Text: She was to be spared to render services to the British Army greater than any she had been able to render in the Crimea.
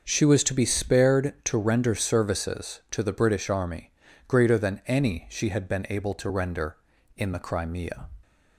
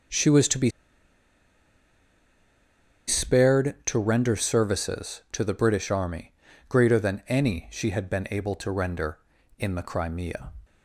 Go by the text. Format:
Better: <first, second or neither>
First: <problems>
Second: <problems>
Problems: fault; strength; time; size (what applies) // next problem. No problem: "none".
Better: first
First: starts louder than the rest; until 1.0 s; 6.5 dB // pauses between "Army" and "greater"; at 3.9 s; 0.38 s long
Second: starts louder than the rest; until 3.5 s; 6.5 dB // pauses between "be" and "spared"; strong; at 0.6 s; 2.3 s long // pauses between "Army" and "greater"; at 6.3 s; 0.38 s long